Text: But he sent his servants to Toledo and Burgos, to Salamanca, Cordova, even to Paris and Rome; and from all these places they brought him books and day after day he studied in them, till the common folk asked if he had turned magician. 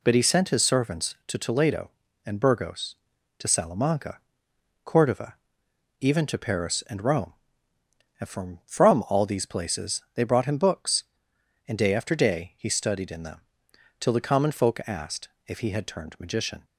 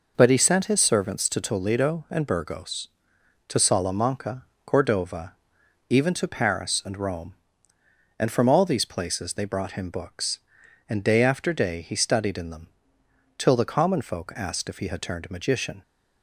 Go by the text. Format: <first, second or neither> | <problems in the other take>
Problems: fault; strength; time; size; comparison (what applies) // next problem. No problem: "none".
second | says "from" twice; at 8.6 s // pauses between "asked" and "if"; slight; at 15.2 s; 0.18 s long